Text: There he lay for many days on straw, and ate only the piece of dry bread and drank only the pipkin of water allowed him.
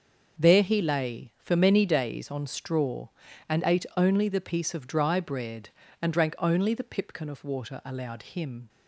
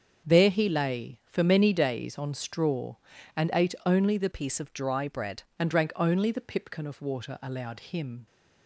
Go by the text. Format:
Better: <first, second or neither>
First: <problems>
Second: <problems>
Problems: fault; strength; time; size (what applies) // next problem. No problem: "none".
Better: first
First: starts louder than the rest; until 1.4 s; 6.5 dB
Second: starts louder than the rest; until 1.3 s; 7 dB // changes voice from "piece" to "bread"; from 4.3 to 5.4 s; 1.1 s long